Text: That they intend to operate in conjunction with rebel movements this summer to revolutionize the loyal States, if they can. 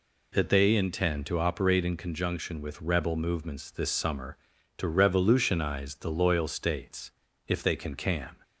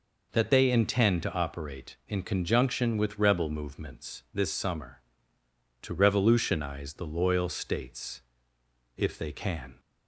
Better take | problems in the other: second | says "can" twice; at 7.9 s

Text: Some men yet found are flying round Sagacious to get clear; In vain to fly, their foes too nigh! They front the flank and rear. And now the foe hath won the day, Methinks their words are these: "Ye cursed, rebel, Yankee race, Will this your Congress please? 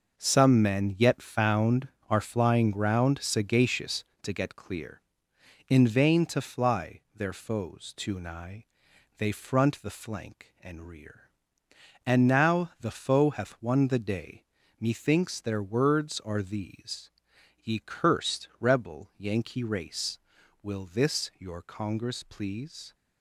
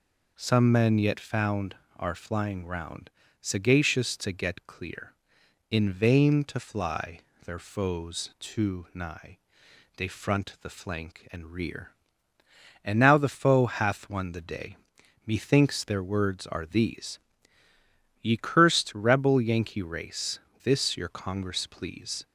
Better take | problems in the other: first | pauses between "round" and "Sagacious"; slight; at 3.0 s; 0.30 s long // skips "Will"; at 20.4 s

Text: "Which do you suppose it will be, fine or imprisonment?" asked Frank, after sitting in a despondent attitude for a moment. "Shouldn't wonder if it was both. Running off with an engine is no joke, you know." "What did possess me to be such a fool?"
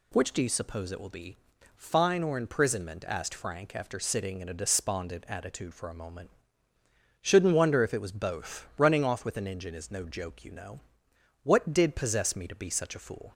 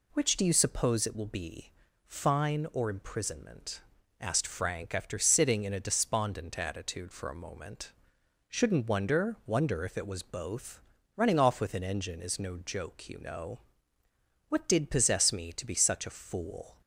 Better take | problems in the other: first | says "wonder" twice; at 9.4 s

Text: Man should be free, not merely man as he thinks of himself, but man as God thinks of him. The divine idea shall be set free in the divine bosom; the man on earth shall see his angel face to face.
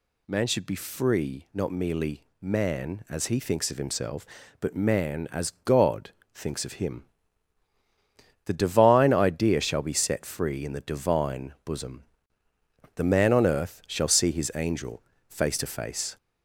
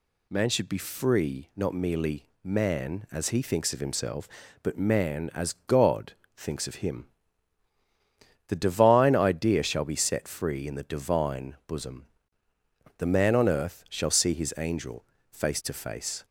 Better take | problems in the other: second | gets louder; slight; throughout; 2.5 dB // pauses between "merely" and "man"; slight; at 2.2 s; 0.16 s long; slight in the second // pauses between "God" and "thinks"; slight; at 6.1 s; 0.22 s long; slight in the second // pauses between "angel" and "face"; slight; at 15.0 s; 0.26 s long; slight in the second

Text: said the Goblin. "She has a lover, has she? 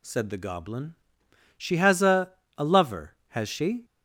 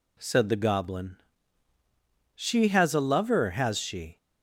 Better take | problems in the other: second | says "a" twice; at 2.5 s

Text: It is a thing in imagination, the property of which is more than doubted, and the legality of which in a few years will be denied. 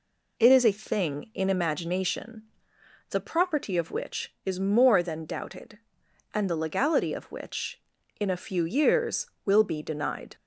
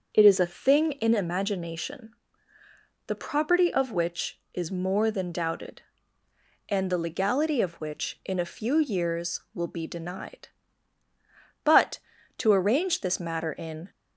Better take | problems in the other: first | starts louder than the rest; until 1.1 s; 6.5 dB // goes on to say "But to arrange this matter in"; strong; from 11.6 s on; 2.2 s long

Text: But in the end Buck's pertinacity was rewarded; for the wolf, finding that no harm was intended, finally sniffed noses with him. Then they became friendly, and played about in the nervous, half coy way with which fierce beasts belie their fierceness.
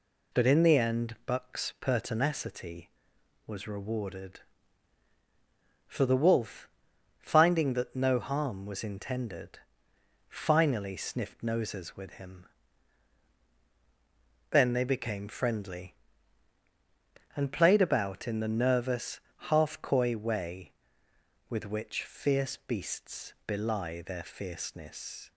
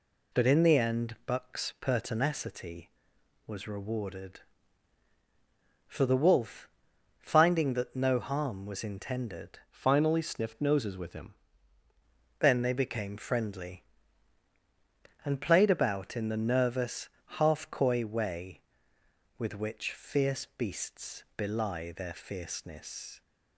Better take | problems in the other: first | changes voice from "finally" to "him"; from 9.6 to 11.3 s; 1.7 s long

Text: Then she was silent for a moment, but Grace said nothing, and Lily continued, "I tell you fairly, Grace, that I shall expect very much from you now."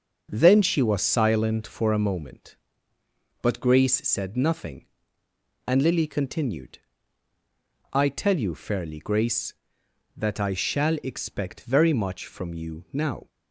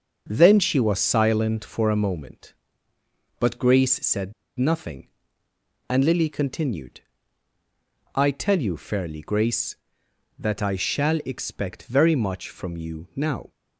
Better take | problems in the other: first | starts louder than the rest; until 1.3 s; 6.5 dB; also in the first // pauses between "said" and "nothing"; slight; at 4.3 s; 0.26 s long

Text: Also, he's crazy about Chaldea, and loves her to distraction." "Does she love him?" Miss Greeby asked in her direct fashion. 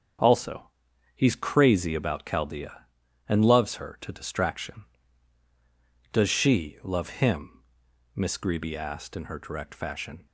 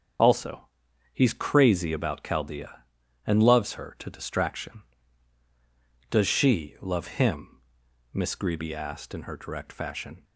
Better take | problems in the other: first | loses the start of "Also"; at 0.1 s; 35 ms // starts louder than the rest; strong; until 1.6 s; 7.5 dB; strong in the first

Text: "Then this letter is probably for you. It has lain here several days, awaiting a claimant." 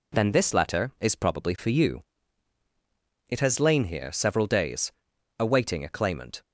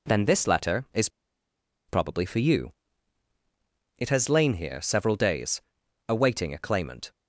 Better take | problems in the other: first | pauses between "is" and "probably"; noticeable; at 1.0 s; 0.79 s long

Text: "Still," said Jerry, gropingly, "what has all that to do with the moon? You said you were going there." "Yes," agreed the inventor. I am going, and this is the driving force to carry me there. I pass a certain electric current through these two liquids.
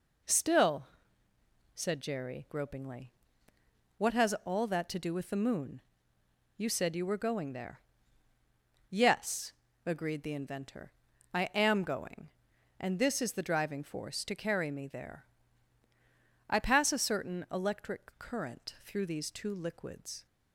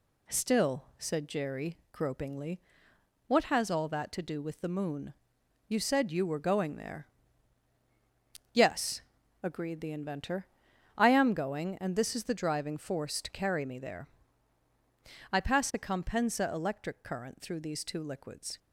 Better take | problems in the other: first | says "compensa" for "certain"; at 15.7 s

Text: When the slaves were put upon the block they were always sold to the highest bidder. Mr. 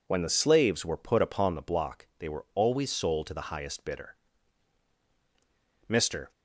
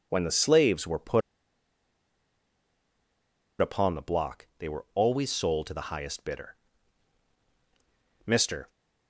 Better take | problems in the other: first | pauses between "put" and "upon"; strong; at 1.2 s; 2.4 s long

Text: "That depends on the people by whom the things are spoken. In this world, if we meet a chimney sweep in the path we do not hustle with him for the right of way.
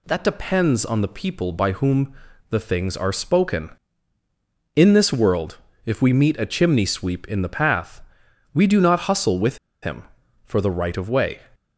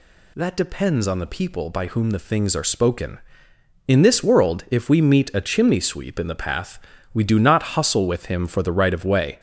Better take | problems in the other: second | pauses between "whom" and "the"; at 2.1 s; 0.38 s long // pauses between "path" and "we"; noticeable; at 8.0 s; 0.52 s long; slight in the second // pauses between "with" and "him"; slight; at 9.5 s; 0.25 s long

